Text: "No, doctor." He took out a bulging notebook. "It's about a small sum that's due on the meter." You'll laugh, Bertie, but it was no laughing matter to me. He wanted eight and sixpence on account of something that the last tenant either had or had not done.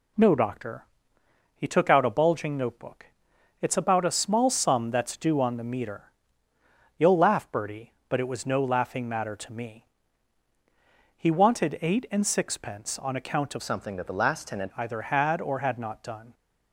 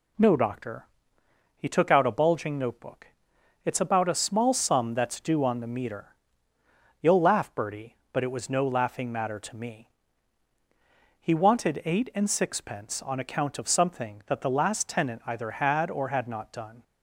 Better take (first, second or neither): second